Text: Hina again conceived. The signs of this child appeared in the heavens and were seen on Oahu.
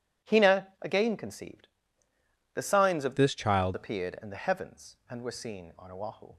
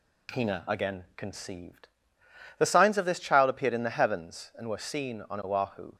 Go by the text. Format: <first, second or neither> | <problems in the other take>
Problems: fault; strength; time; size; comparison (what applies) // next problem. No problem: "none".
second | changes voice from "this" to "child"; from 3.1 to 3.7 s; 0.6 s long